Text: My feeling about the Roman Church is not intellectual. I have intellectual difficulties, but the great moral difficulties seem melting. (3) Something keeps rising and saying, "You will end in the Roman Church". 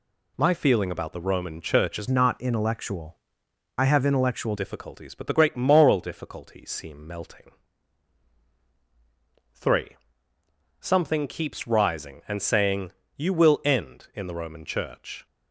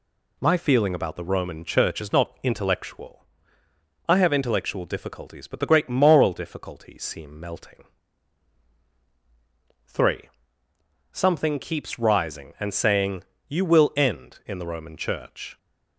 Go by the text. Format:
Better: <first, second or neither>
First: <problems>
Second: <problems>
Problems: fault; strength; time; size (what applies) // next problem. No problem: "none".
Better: second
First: changes voice from "not" to "intellectual"; from 2.0 to 4.5 s; 2.5 s long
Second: none